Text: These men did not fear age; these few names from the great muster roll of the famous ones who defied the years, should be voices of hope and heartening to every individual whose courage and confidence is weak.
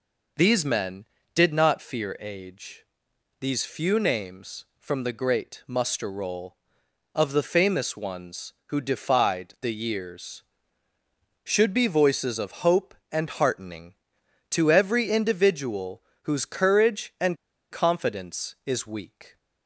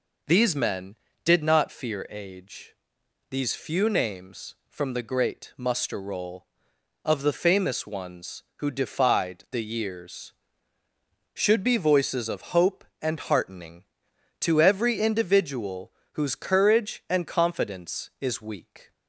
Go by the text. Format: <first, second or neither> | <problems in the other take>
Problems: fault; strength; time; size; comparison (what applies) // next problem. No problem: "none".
second | pauses between "individual" and "whose"; slight; at 16.0 s; 0.22 s long; slight in the second // pauses between "and" and "confidence"; slight; at 17.3 s; 0.34 s long